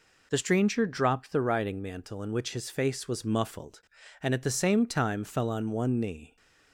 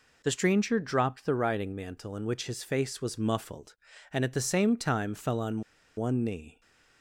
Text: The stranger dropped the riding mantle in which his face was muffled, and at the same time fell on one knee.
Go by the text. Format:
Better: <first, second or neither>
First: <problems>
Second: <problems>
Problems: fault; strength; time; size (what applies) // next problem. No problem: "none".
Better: first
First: none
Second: pauses between "on" and "one"; at 5.6 s; 0.36 s long